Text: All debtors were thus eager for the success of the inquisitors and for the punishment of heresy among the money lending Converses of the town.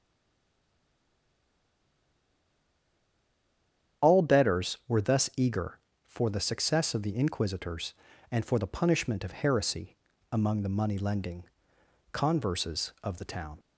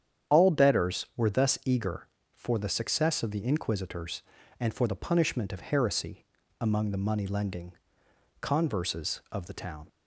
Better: second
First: stays silent before the first word; strong; until 4.0 s; 4.0 s long // starts louder than the rest; strong; until 5.1 s; 9 dB // pauses between "heresy" and "among"; slight; at 9.9 s; 0.34 s long // pauses between "lending" and "Converses"; noticeable; at 11.4 s; 0.68 s long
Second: starts louder than the rest; strong; until 1.3 s; 9 dB // pauses between "heresy" and "among"; slight; at 6.2 s; 0.34 s long // pauses between "lending" and "Converses"; noticeable; at 7.7 s; 0.68 s long

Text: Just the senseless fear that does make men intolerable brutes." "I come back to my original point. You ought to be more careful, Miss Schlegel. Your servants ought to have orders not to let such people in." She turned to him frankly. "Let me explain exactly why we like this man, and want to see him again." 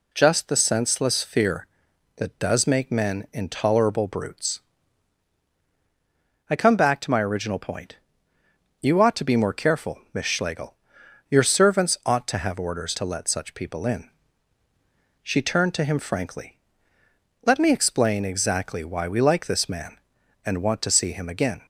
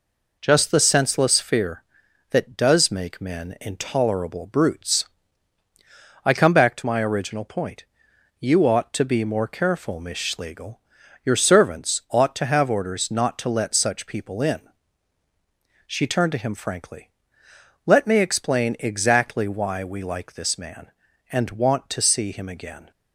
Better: second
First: skips "not"; at 12.9 s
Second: none

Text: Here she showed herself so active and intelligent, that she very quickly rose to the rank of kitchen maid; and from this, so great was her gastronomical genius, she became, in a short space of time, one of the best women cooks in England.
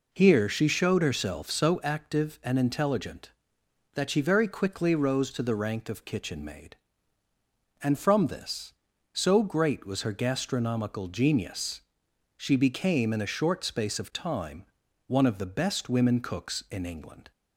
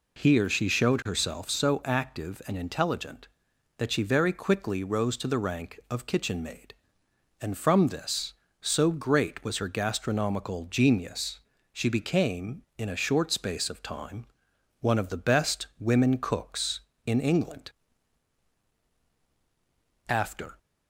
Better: first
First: none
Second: goes on to say "After"; slight; from 20.0 s on; 0.48 s long

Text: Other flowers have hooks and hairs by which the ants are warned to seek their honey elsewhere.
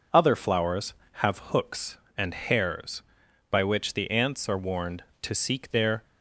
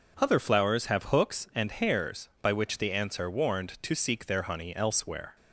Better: second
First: stops before "honey elsewhere"; at 6.0 s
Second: none

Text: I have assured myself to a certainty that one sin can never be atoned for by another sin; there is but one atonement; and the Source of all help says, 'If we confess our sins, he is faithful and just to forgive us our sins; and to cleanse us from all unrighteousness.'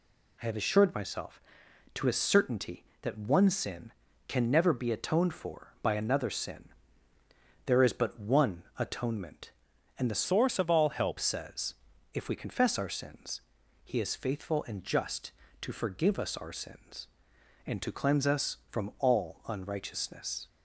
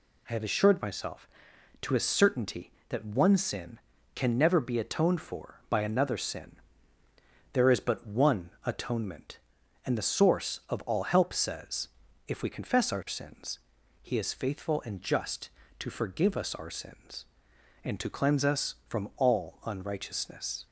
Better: second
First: pauses between "one" and "atonement"; slight; at 8.6 s; 0.16 s long // changes voice from "Source" to "help"; from 10.2 to 11.1 s; 0.9 s long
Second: pauses between "one" and "atonement"; slight; at 8.4 s; 0.16 s long

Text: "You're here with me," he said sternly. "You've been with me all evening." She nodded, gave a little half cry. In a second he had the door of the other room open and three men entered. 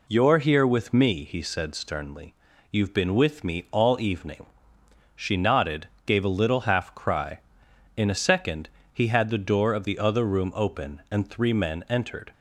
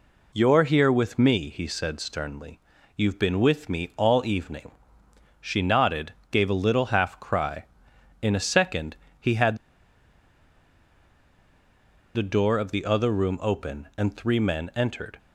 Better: first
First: pauses between "second" and "he"; slight; at 8.6 s; 0.22 s long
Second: pauses between "second" and "he"; slight; at 8.9 s; 0.22 s long // pauses between "had" and "the"; strong; at 9.5 s; 2.5 s long

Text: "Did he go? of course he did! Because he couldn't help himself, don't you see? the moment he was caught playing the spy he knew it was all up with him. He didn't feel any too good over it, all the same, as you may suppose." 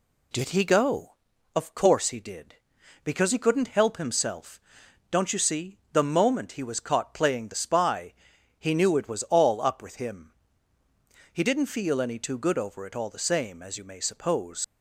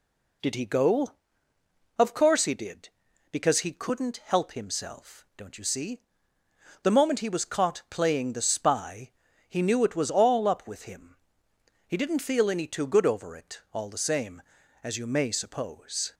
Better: second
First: pauses between "spy" and "he"; at 8.1 s; 0.44 s long // leaves "suppose" unfinished; at 14.6 s; 50 ms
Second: pauses between "spy" and "he"; slight; at 9.1 s; 0.36 s long

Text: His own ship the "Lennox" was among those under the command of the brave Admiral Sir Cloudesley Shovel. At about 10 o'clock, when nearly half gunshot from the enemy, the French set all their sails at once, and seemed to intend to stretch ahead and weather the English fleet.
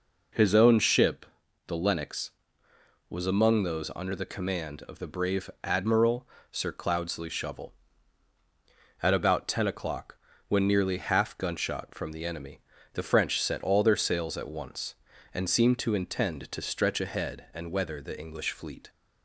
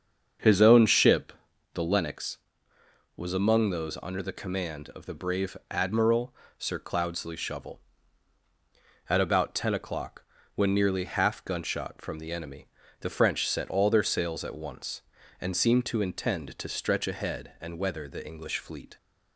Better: first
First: pauses between "ship" and "the"; at 1.2 s; 0.42 s long // pauses between "brave" and "Admiral"; slight; at 5.4 s; 0.16 s long // pauses between "Admiral" and "Sir"; slight; at 6.2 s; 0.22 s long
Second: starts louder than the rest; until 2.1 s; 7 dB // pauses between "ship" and "the"; at 1.3 s; 0.42 s long // pauses between "brave" and "Admiral"; slight; at 5.5 s; 0.16 s long // pauses between "Admiral" and "Sir"; slight; at 6.3 s; 0.22 s long

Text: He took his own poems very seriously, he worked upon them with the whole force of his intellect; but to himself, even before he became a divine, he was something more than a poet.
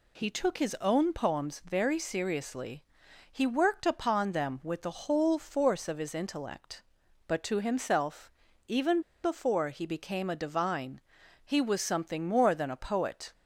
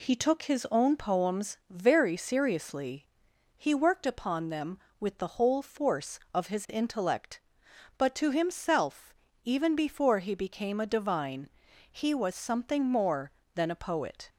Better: second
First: pauses between "even" and "before"; slight; at 9.0 s; 0.21 s long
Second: none

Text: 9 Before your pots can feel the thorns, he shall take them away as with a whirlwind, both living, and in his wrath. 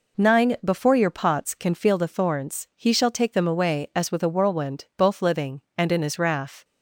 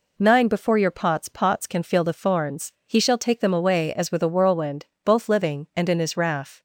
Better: first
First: none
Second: says "pots" twice; at 1.2 s

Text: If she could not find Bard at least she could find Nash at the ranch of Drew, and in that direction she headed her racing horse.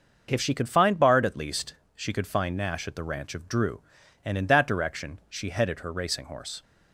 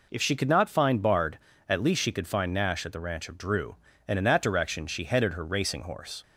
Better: second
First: starts louder than the rest; noticeable; until 1.3 s; 6 dB // skips "not"; at 0.6 s // pauses between "least" and "she"; slight; at 1.7 s; 0.22 s long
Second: none

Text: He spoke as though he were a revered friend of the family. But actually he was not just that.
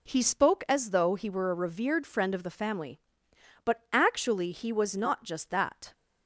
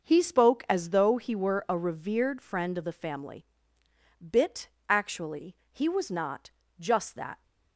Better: first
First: none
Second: says "Bit" for "But"; at 4.2 s // pauses between "actually" and "he"; slight; at 5.5 s; 0.16 s long // pauses between "not" and "just"; slight; at 6.5 s; 0.28 s long

